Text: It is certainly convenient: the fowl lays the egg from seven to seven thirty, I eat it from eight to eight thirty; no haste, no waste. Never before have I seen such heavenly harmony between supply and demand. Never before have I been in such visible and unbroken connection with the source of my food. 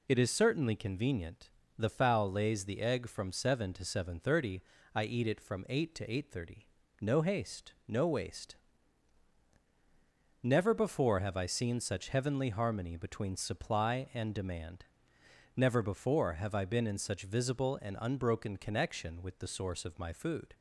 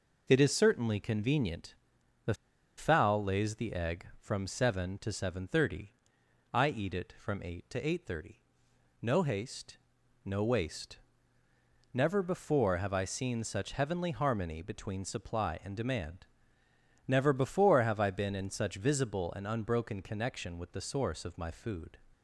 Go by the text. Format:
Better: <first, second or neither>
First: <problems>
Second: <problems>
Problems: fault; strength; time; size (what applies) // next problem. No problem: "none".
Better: first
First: none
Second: pauses between "the" and "fowl"; at 2.3 s; 0.43 s long